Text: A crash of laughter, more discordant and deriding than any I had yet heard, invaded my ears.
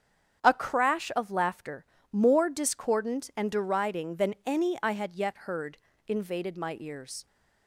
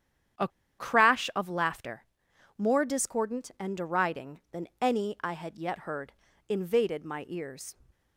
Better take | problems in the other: first | starts louder than the rest; strong; until 1.7 s; 9.5 dB; strong in the first // pauses between "A" and "crash"; slight; at 0.4 s; 0.30 s long

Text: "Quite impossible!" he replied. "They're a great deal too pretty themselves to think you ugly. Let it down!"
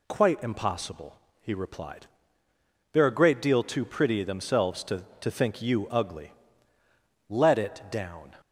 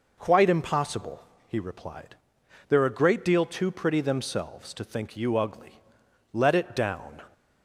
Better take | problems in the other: second | says "to" twice; at 5.2 s

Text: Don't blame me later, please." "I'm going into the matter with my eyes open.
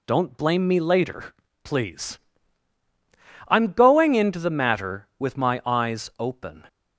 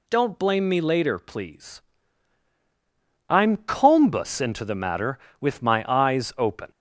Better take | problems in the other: first | says "combus" for "going"; at 3.5 s

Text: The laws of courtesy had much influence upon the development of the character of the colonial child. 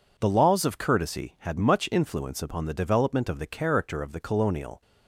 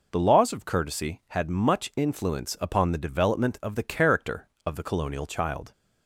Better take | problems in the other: second | stops before "child"; at 4.8 s

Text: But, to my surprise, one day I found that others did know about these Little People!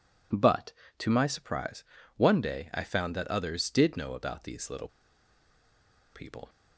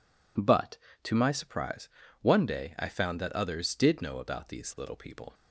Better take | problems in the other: second | pauses between "Little" and "People"; strong; at 4.8 s; 1.2 s long

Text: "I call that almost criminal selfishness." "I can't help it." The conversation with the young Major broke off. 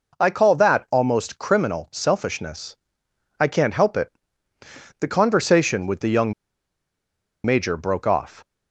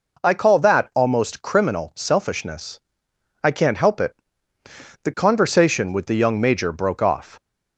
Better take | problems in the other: second | pauses between "young" and "Major"; at 6.3 s; 1.1 s long

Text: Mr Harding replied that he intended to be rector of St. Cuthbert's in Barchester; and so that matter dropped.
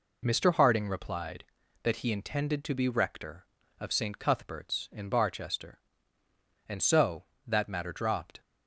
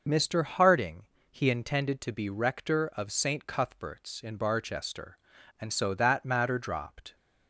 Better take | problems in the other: first | skips "replied that"; at 1.1 s

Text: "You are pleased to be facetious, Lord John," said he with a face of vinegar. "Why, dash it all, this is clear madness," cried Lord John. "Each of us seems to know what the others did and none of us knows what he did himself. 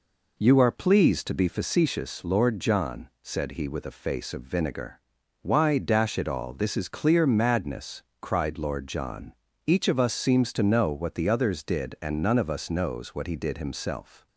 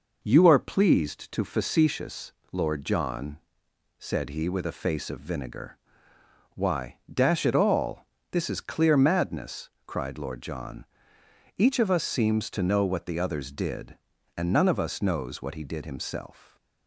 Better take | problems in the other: first | skips "be"; at 1.4 s

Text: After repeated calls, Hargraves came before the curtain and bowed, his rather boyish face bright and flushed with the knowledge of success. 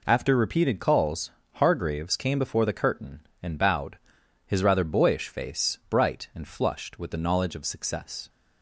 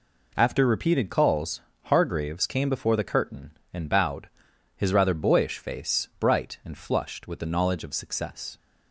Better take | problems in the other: neither | none

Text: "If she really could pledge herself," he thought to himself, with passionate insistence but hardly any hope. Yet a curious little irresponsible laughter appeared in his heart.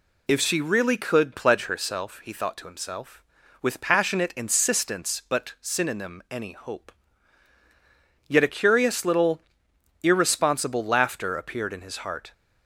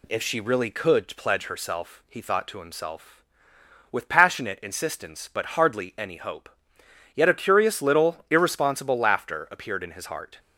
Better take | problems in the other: second | says "synonym" for "hardly"; at 5.6 s // pauses between "little" and "irresponsible"; noticeable; at 9.4 s; 0.60 s long

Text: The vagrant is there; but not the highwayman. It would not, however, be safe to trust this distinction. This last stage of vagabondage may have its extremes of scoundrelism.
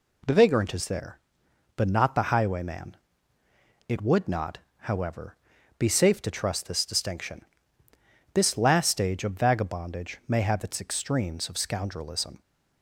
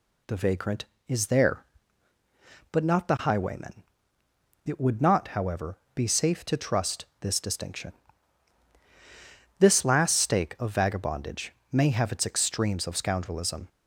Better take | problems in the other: first | pauses between "trust" and "this"; slight; at 7.0 s; 0.16 s long // says "stake" for "stage"; at 10.1 s // pauses between "vagabondage" and "may"; slight; at 11.5 s; 0.18 s long

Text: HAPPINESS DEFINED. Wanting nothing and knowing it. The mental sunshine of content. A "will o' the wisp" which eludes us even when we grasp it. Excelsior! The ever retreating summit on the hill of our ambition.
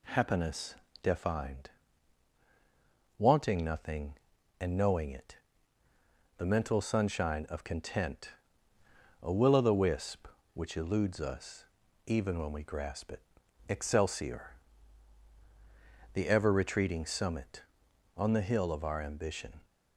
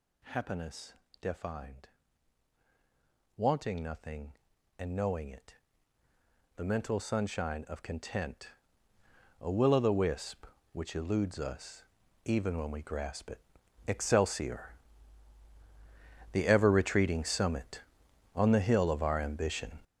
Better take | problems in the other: first | gets louder; strong; throughout; 10 dB // pauses between "HAPPINESS" and "DEFINED"; slight; at 0.9 s; 0.26 s long; slight in the first // pauses between "us" and "even"; at 11.8 s; 0.42 s long; also in the first

